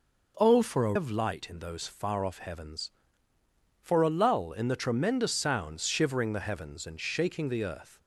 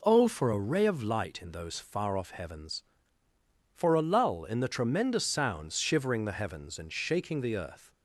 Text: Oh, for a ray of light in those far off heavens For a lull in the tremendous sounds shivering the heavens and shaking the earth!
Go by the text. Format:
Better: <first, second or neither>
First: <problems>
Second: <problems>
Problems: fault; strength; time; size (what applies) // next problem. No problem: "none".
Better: second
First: skips "ray"; at 0.9 s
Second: none